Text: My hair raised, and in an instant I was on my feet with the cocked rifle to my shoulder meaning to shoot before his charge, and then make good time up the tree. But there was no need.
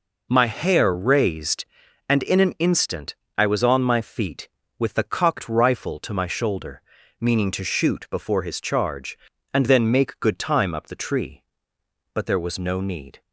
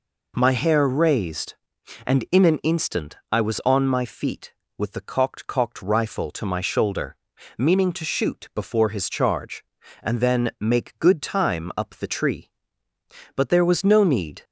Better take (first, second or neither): first